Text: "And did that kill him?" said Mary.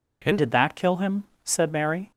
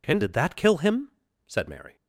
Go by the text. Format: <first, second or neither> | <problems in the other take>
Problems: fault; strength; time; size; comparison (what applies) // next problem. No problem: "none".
second | changes voice at "did"; from 0.3 s on; 1.8 s long